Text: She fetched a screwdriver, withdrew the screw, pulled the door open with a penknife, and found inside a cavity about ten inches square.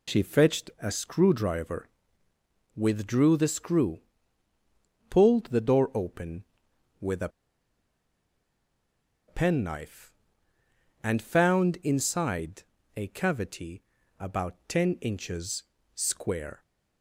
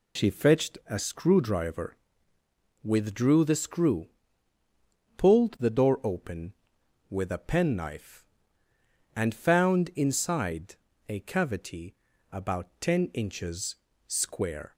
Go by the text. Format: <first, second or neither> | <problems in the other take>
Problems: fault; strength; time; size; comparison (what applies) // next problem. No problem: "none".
second | pauses between "a" and "penknife"; strong; at 7.2 s; 1.9 s long // pauses between "inside" and "a"; slight; at 12.6 s; 0.34 s long; slight in the second // pauses between "cavity" and "about"; at 13.8 s; 0.38 s long; also in the second // pauses between "inches" and "square"; slight; at 15.6 s; 0.32 s long; slight in the second